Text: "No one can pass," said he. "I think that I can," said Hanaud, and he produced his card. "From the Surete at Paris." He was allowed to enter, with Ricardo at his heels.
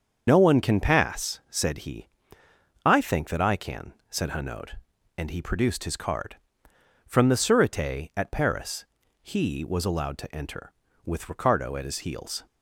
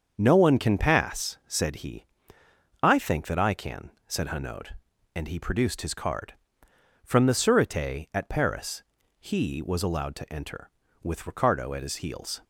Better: second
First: loses the start of "No"; at 0.2 s; 80 ms // starts louder than the rest; until 1.2 s; 7 dB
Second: starts louder than the rest; until 1.1 s; 7 dB

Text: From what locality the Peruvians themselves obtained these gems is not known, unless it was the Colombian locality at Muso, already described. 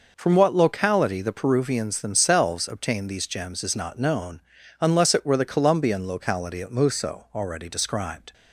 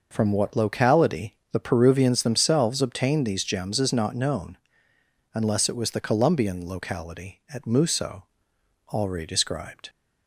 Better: second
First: says "were" for "was"; at 5.2 s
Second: none

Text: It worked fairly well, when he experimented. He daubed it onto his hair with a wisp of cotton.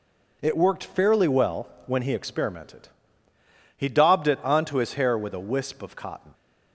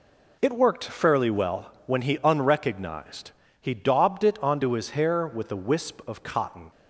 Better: first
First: none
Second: says "unrecognized" for "experimented"; at 2.2 s

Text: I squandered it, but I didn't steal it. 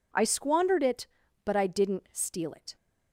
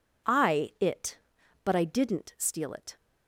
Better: first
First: none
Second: skips "squandered"; at 0.7 s

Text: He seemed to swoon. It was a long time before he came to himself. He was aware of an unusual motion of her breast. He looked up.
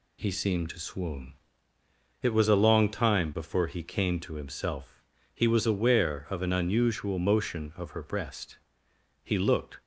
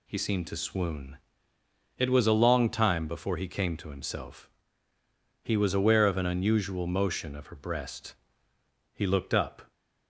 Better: second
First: stops before "up"; at 9.8 s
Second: none

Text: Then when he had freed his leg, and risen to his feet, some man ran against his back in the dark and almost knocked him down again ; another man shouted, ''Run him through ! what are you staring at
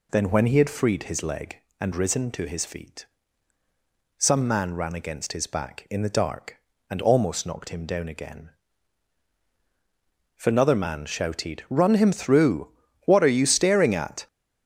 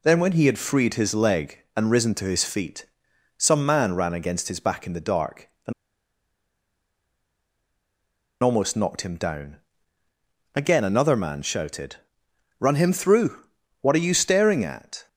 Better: first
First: none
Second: pauses between "and" and "almost"; strong; at 5.7 s; 2.7 s long // pauses between "down" and "again"; noticeable; at 9.5 s; 0.96 s long

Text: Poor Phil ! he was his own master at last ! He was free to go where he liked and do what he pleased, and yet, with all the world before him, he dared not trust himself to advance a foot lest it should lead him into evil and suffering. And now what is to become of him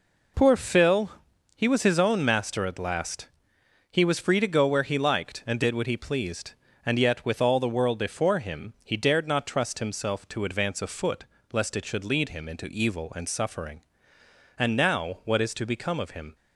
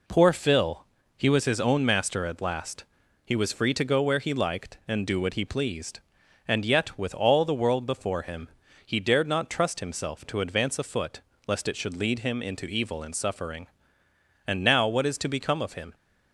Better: second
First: says "did" for "do"; at 5.6 s // pauses between "foot" and "lest"; slight; at 11.2 s; 0.30 s long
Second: pauses between "foot" and "lest"; slight; at 11.2 s; 0.24 s long

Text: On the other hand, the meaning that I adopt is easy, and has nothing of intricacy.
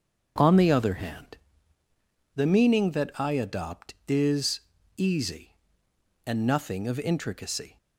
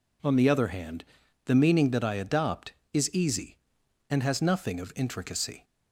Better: second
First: starts louder than the rest; until 1.3 s; 7 dB // pauses between "is" and "easy"; slight; at 4.6 s; 0.34 s long // skips "has"; at 6.4 s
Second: none

